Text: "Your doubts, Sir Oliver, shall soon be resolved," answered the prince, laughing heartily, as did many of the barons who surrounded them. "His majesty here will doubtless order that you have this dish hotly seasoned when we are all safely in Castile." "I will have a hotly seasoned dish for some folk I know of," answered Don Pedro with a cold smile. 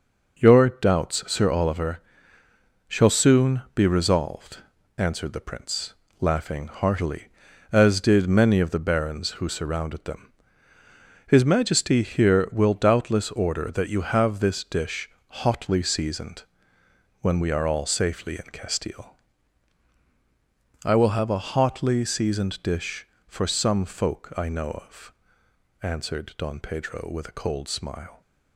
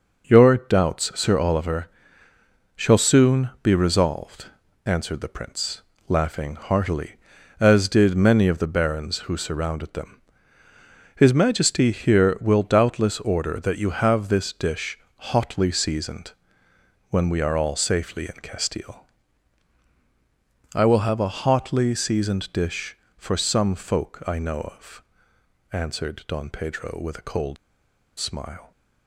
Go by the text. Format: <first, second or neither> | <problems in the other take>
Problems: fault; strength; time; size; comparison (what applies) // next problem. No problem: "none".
first | pauses between "dish" and "hotly"; slight; at 14.9 s; 0.20 s long; slight in the first // pauses between "seasoned" and "when"; noticeable; at 16.3 s; 0.80 s long; noticeable in the first // pauses between "cold" and "smile"; noticeable; at 27.5 s; 0.62 s long